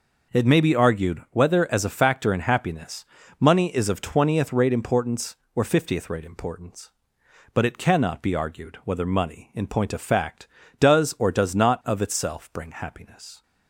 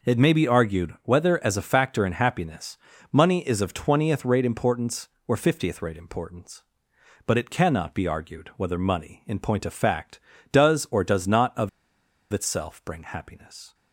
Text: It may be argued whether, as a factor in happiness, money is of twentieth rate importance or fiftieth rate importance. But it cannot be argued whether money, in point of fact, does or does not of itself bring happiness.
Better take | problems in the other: first | pauses between "of" and "itself"; noticeable; at 11.6 s; 0.62 s long

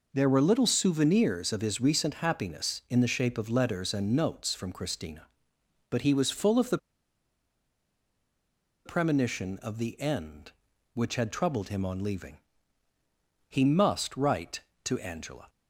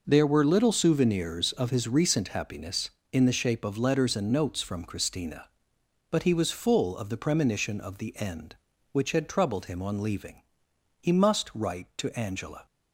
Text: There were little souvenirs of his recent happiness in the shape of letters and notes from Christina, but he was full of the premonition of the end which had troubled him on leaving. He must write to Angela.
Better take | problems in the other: second | pauses between "the" and "premonition"; strong; at 6.7 s; 2.0 s long

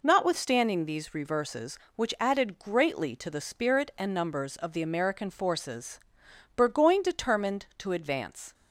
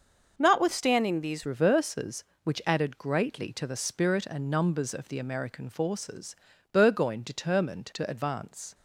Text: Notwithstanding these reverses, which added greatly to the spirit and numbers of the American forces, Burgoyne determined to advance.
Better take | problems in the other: first | starts louder than the rest; noticeable; until 1.3 s; 6 dB // changes voice at "reverses"; from 1.4 s on; 7.3 s long

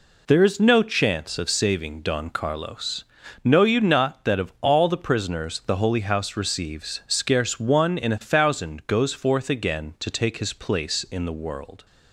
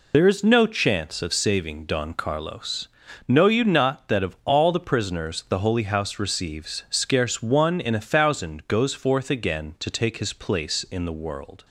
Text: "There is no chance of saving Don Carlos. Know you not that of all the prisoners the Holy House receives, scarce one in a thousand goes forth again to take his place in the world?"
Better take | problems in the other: first | loses the start of "There"; at 0.1 s; 40 ms

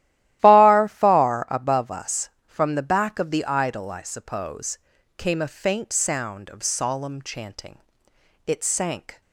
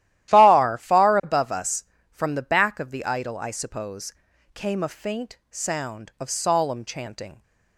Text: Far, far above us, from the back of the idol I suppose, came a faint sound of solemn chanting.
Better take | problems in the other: second | starts louder than the rest; strong; until 1.4 s; 14.5 dB; strong in the second // goes on to say "It sank"; noticeable; from 8.4 s on; 0.74 s long

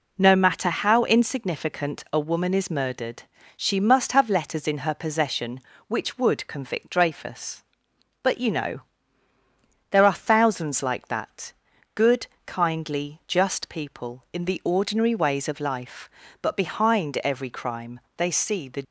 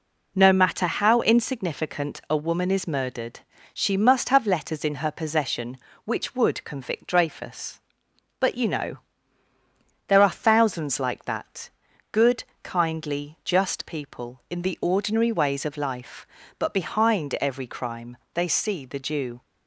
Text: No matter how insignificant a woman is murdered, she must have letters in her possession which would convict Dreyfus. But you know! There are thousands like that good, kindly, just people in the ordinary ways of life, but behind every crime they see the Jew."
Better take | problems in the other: second | pauses between "that" and "good"; at 11.5 s; 0.42 s long; also in the second // pauses between "crime" and "they"; slight; at 18.0 s; 0.16 s long; slight in the second // stops before "Jew"; at 18.8 s

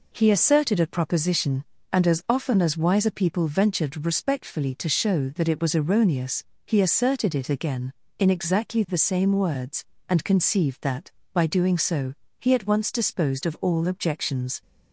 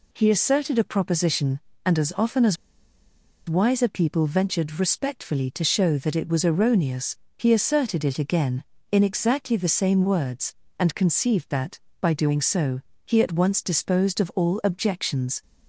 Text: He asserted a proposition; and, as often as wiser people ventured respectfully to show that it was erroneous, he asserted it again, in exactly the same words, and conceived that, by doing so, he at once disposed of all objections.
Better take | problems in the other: first | pauses between "as" and "wiser"; noticeable; at 2.5 s; 0.93 s long

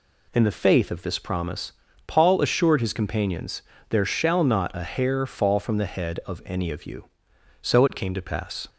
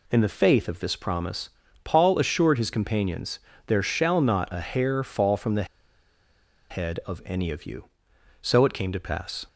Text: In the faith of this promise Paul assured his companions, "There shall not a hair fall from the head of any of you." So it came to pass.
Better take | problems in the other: first | pauses between "promise" and "Paul"; slight; at 1.4 s; 0.34 s long; slight in the first // pauses between "the" and "head"; at 5.6 s; 1.0 s long

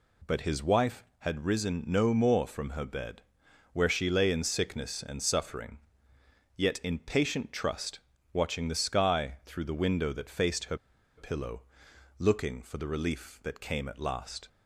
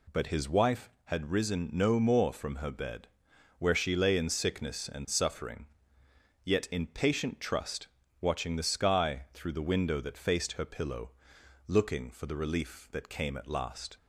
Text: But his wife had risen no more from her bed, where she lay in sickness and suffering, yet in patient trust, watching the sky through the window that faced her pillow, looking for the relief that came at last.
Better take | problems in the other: second | pauses between "her" and "pillow"; at 10.7 s; 0.40 s long

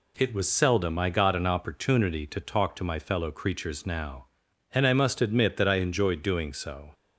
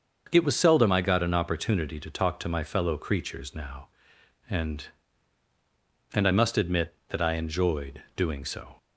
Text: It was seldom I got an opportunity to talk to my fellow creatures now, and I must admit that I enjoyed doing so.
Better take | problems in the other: first | starts louder than the rest; until 1.3 s; 6.5 dB // says "and" twice; at 6.1 s

